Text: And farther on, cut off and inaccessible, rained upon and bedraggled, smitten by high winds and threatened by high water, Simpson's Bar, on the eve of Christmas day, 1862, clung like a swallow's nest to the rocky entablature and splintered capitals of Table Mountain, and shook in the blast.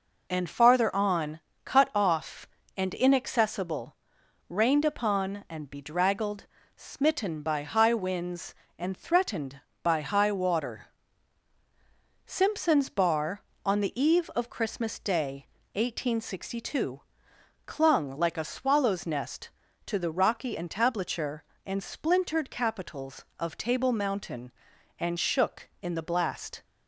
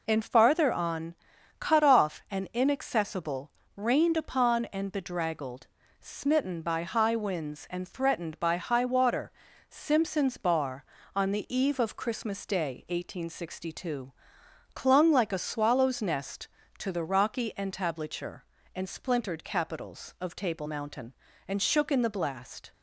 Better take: neither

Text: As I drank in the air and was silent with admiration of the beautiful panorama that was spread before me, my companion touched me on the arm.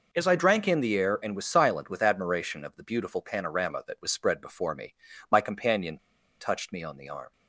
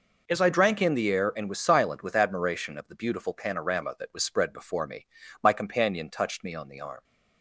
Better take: second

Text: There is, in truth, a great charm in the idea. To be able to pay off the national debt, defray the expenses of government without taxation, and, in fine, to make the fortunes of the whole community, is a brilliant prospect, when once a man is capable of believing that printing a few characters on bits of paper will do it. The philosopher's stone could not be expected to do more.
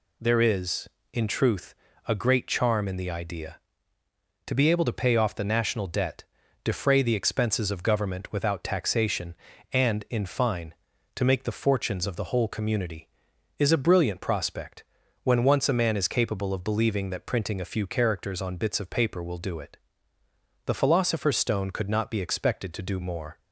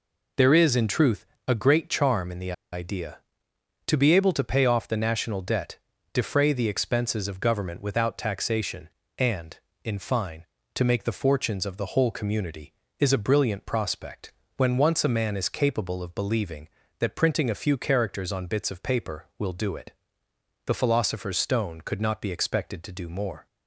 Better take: first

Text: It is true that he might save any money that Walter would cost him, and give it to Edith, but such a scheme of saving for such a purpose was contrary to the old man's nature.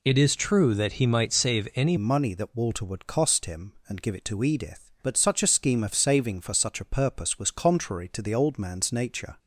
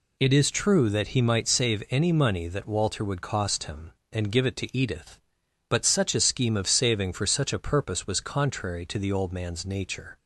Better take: second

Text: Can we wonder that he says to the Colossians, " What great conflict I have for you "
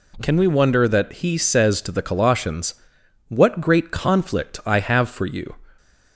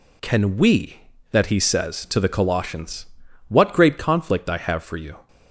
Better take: first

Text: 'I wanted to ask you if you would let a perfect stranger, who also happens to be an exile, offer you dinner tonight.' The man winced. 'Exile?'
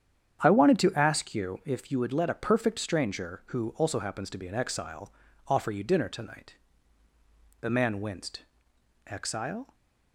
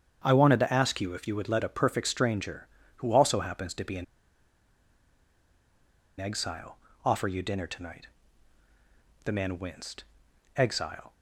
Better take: first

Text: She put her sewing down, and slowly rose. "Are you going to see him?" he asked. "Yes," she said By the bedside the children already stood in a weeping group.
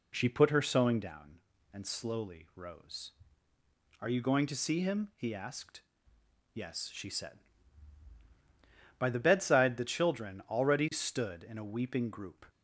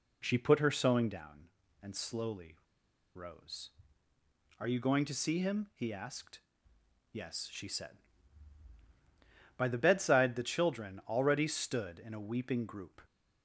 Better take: first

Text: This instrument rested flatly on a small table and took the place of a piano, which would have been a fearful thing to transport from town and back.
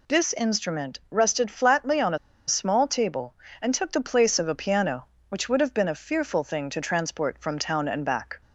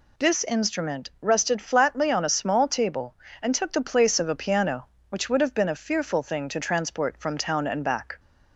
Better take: second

